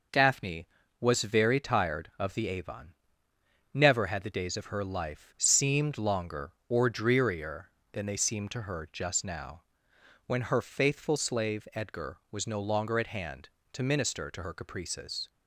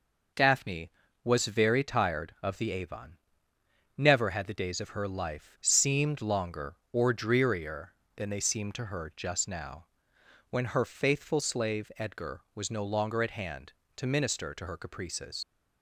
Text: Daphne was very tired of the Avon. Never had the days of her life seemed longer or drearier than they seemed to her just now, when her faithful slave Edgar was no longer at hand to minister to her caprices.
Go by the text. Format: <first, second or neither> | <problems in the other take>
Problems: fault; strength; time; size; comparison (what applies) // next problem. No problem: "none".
first | leaves "caprices" unfinished; at 15.4 s; 100 ms